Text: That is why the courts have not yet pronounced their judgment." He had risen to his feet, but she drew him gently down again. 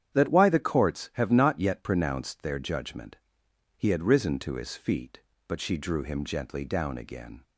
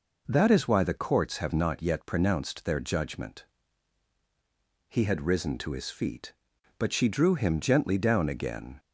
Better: second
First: starts louder than the rest; strong; until 1.1 s; 9 dB // skips "is"; at 0.2 s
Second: none

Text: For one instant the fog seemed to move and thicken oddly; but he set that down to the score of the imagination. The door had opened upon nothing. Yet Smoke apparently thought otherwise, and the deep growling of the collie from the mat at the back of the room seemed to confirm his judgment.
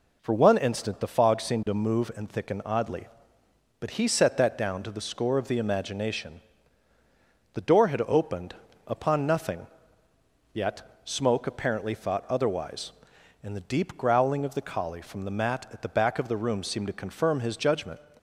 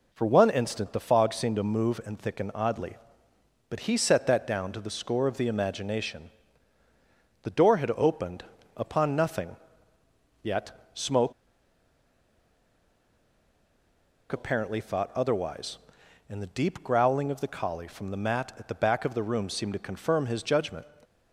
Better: first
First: pauses between "opened" and "upon"; slight; at 8.5 s; 0.32 s long // pauses between "Yet" and "Smoke"; slight; at 10.8 s; 0.22 s long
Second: pauses between "opened" and "upon"; slight; at 8.4 s; 0.32 s long // pauses between "Yet" and "Smoke"; slight; at 10.7 s; 0.22 s long // pauses between "Smoke" and "apparently"; strong; at 11.3 s; 2.9 s long

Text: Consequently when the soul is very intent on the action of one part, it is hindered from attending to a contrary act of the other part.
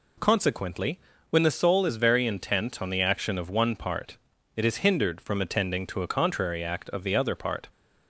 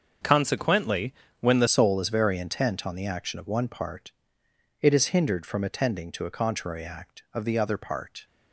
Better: first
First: pauses between "Consequently" and "when"; slight; at 0.9 s; 0.32 s long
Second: starts louder than the rest; until 1.5 s; 6.5 dB // pauses between "Consequently" and "when"; slight; at 1.1 s; 0.26 s long // changes voice at "soul"; from 1.6 s on; 6.6 s long

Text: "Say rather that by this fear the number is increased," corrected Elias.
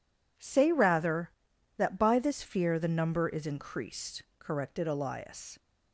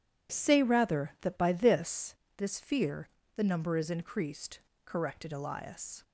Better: first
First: none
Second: says "this" twice; at 2.3 s // pauses between "fear" and "the"; slight; at 3.0 s; 0.26 s long

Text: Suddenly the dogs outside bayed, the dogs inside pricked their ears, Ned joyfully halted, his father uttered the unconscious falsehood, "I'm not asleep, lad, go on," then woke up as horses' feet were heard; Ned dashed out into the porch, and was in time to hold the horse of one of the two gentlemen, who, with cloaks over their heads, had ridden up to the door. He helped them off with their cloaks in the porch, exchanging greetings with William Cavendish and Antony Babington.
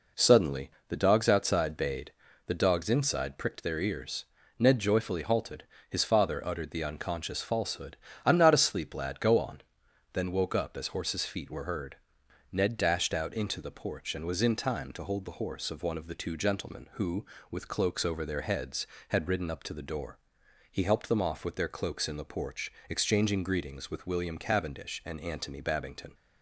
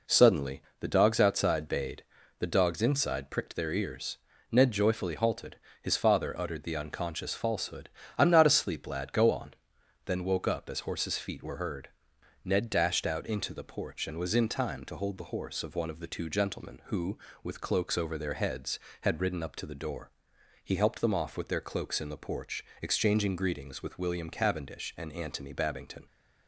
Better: neither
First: pauses between "Suddenly" and "the"; slight; at 0.7 s; 0.16 s long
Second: pauses between "Suddenly" and "the"; slight; at 0.6 s; 0.16 s long

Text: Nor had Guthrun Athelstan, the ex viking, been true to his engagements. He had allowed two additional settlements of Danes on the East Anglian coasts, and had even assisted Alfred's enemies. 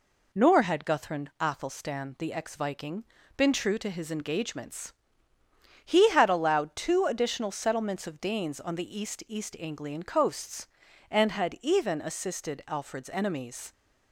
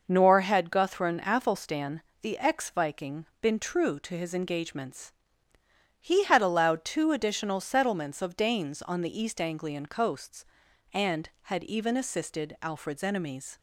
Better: second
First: says "East" twice; at 9.2 s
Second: none

